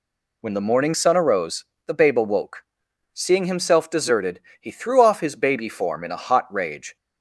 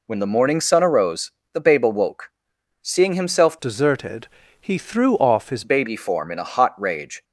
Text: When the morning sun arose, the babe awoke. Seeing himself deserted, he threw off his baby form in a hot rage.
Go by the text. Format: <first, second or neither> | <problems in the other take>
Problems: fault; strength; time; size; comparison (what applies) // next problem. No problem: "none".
first | changes voice from "deserted" to "his"; from 3.6 to 5.6 s; 2.0 s long